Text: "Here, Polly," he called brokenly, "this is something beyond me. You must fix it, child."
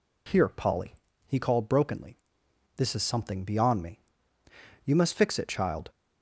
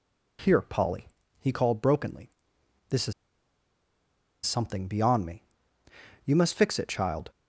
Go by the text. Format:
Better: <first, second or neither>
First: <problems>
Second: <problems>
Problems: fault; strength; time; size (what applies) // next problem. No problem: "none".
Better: first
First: none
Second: pauses between "is" and "something"; strong; at 3.1 s; 1.3 s long